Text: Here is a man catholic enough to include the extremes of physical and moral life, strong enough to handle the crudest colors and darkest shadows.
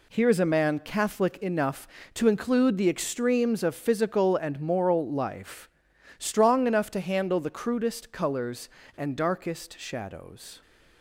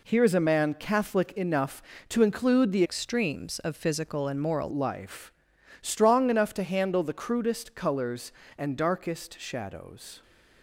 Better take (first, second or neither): first